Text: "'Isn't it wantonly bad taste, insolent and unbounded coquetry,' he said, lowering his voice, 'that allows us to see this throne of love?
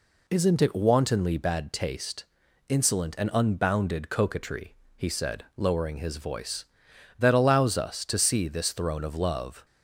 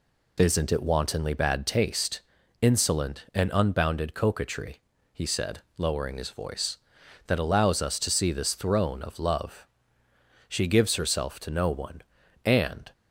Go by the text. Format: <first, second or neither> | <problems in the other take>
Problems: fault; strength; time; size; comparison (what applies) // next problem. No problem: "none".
first | goes on to say "She gives herself to no one and"; strong; from 10.4 s on; 2.4 s long